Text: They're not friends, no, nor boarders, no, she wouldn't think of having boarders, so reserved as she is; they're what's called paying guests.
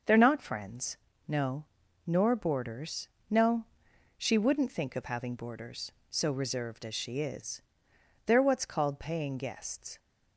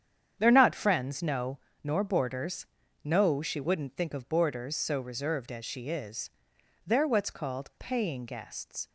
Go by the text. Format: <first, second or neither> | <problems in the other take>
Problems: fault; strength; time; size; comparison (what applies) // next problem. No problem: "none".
first | starts louder than the rest; strong; until 1.3 s; 8.5 dB; also in the first // skips "having"; at 4.2 s